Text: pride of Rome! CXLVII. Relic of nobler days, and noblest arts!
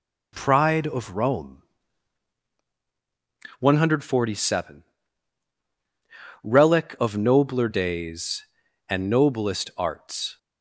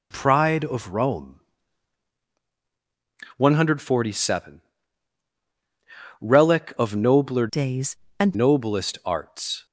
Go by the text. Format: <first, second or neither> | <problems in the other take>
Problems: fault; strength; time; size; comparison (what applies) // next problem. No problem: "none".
first | changes voice from "days" to "and"; from 7.4 to 8.3 s; 0.9 s long